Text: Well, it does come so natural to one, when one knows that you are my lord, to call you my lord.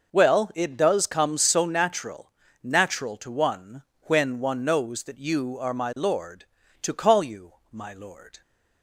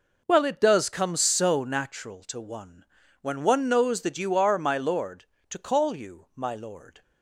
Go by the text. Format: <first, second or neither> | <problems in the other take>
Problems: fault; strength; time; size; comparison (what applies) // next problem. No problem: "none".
second | says "natural" twice; at 2.6 s // pauses between "you" and "my"; slight; at 7.5 s; 0.20 s long